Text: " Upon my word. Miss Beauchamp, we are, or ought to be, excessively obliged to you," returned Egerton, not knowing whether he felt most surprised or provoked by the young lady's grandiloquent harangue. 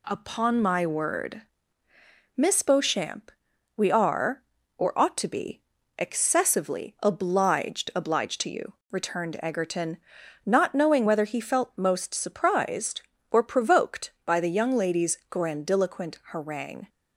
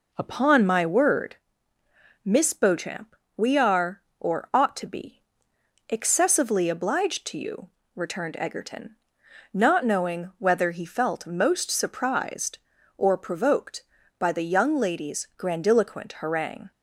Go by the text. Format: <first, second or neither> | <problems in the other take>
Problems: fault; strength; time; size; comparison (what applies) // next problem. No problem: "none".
second | says "obliged" twice; at 7.9 s